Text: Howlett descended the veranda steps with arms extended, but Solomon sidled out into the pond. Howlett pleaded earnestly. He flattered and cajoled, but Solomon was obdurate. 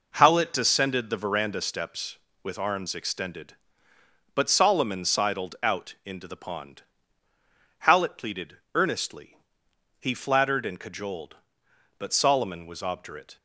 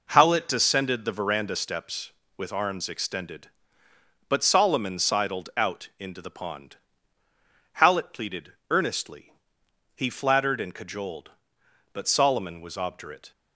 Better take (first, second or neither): neither